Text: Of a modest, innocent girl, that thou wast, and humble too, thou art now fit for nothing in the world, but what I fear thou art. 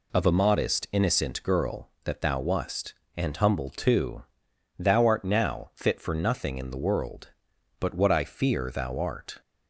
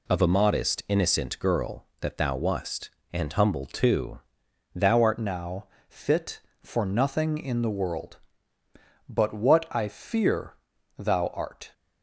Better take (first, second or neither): first